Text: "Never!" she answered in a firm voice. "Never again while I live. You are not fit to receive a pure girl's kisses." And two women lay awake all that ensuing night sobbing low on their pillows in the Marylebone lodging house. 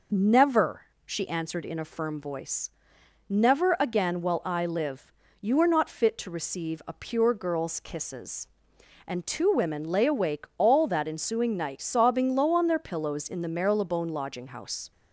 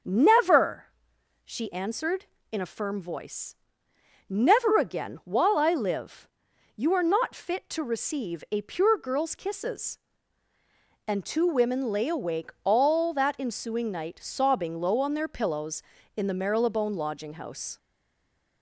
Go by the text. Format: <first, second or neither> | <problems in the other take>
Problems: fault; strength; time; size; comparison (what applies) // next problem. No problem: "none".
first | starts louder than the rest; until 1.6 s; 6.5 dB // stays silent after the last word; slight; from 17.7 s on; 0.9 s long